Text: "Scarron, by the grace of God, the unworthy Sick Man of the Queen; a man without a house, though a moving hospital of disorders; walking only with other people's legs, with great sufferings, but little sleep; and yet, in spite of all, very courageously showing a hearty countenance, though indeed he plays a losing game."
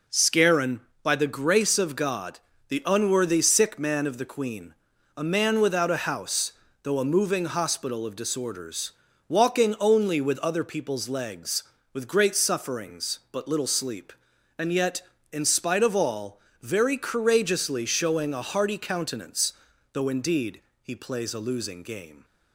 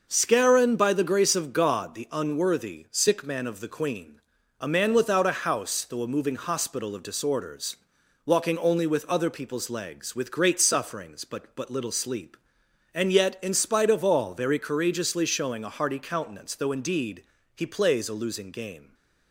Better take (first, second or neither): first